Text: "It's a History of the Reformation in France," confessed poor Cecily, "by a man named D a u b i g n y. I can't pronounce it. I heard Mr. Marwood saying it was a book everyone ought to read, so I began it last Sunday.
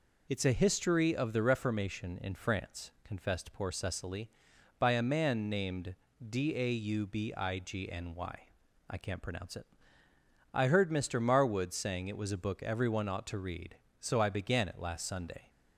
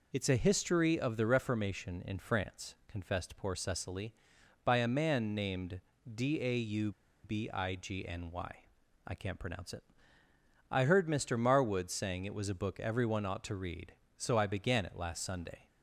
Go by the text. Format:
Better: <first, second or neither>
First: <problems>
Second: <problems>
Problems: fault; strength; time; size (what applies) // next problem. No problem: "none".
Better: first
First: pauses between "named" and "D"; slight; at 5.9 s; 0.28 s long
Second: pauses between "named" and "D"; slight; at 5.8 s; 0.28 s long // pauses between "u" and "b"; slight; at 6.9 s; 0.32 s long